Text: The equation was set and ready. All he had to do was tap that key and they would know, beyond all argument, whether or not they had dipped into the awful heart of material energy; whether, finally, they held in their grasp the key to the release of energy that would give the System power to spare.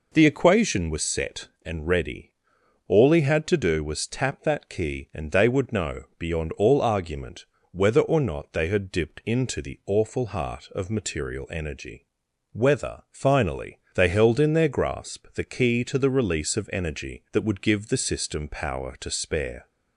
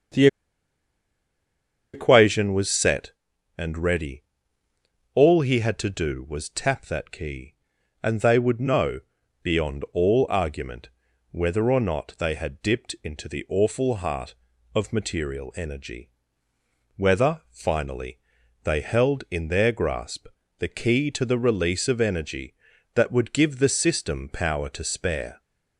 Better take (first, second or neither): first